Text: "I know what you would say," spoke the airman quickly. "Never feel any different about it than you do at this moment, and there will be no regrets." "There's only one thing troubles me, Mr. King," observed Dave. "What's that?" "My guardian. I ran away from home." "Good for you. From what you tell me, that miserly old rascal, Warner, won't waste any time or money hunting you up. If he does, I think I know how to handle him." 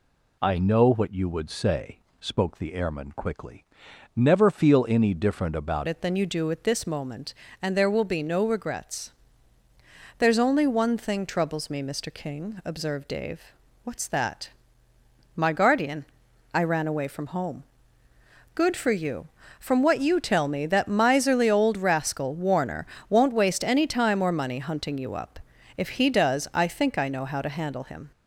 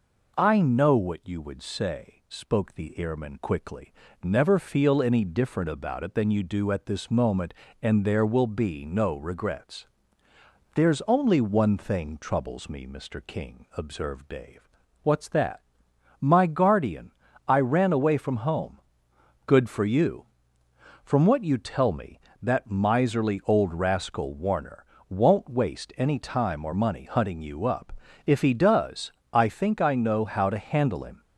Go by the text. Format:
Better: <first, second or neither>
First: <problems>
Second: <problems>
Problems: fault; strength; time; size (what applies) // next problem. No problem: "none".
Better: second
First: changes voice at "it"; from 5.8 s on; 22.3 s long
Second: none